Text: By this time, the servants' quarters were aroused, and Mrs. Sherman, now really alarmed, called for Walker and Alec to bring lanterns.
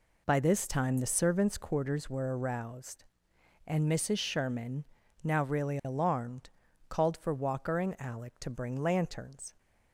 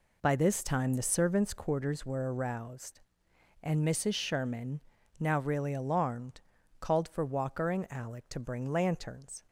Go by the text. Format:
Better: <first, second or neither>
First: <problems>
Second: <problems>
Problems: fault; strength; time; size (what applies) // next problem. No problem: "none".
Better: neither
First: none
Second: none